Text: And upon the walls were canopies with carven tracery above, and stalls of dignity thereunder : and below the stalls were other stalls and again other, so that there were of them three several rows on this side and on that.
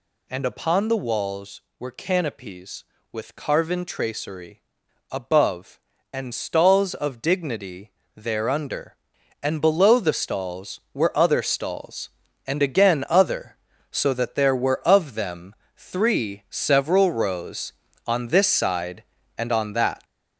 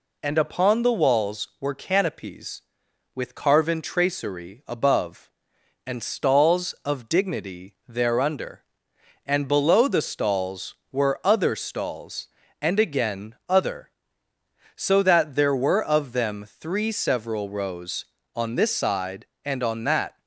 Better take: second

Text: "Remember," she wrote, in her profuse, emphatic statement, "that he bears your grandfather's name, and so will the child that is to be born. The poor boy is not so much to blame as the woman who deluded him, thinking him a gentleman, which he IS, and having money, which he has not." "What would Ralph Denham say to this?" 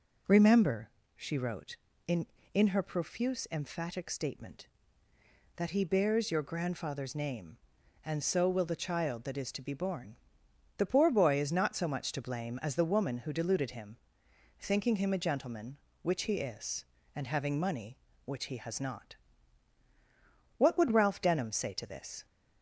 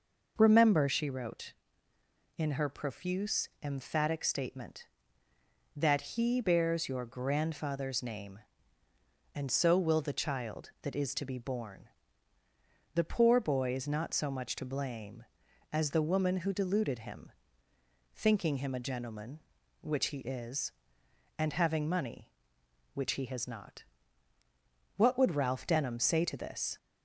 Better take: second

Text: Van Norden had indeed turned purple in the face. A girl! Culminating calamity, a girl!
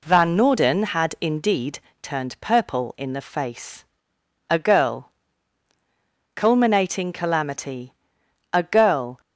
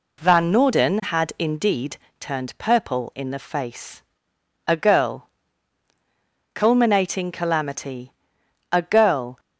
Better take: neither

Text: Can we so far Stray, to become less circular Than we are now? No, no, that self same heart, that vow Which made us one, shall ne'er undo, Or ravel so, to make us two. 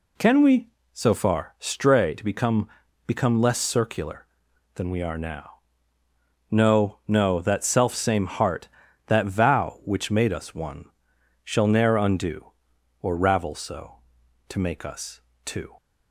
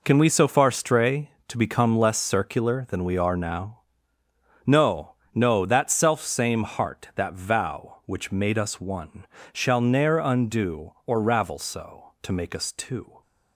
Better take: second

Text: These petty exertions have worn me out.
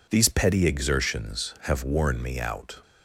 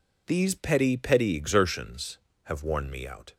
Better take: first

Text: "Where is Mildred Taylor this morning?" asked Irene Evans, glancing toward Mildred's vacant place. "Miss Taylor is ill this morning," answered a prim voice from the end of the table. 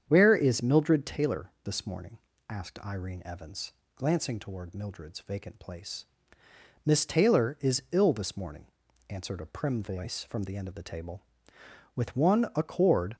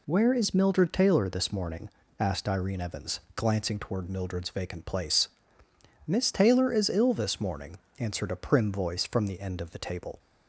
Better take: second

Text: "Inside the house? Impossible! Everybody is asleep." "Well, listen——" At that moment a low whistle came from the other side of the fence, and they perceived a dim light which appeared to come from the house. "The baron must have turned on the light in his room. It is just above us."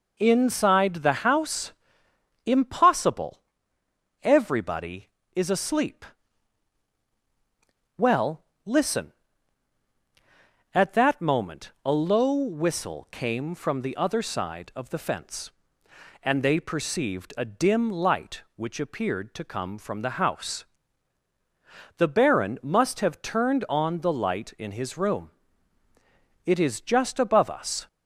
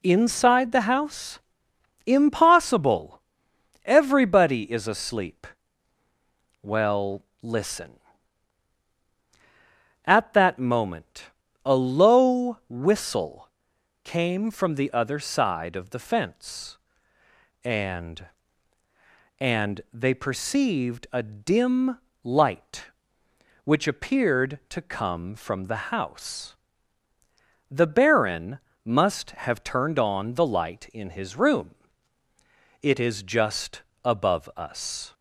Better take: first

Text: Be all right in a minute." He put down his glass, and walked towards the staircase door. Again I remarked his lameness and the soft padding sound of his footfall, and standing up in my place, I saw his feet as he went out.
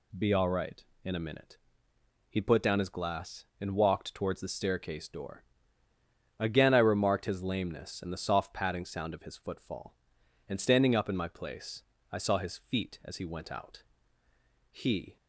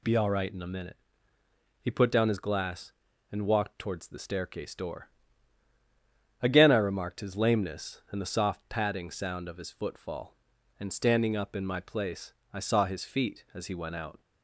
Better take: second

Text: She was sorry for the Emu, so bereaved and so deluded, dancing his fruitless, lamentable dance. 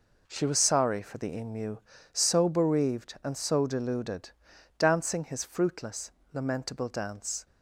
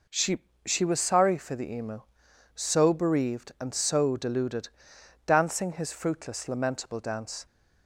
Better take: first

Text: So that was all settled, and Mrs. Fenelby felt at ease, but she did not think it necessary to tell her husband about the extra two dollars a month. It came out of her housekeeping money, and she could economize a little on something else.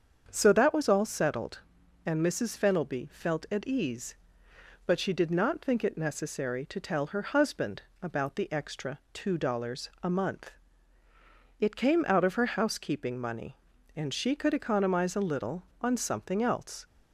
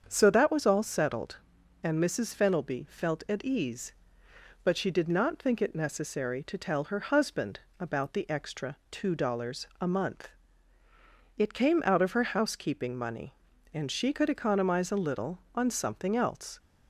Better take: neither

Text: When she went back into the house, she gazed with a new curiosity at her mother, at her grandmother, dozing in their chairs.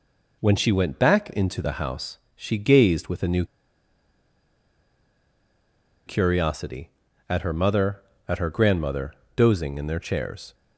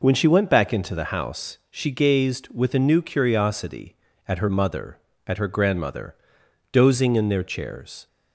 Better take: second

